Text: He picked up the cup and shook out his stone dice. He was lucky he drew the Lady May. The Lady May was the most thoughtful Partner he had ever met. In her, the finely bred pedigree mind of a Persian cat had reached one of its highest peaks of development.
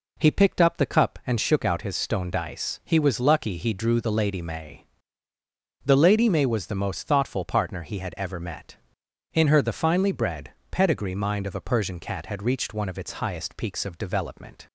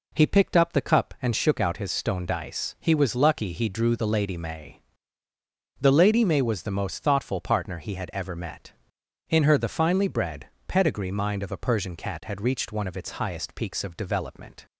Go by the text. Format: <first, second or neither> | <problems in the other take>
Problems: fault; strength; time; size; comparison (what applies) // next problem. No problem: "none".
neither | pauses between "bred" and "pedigree"; slight; the same in both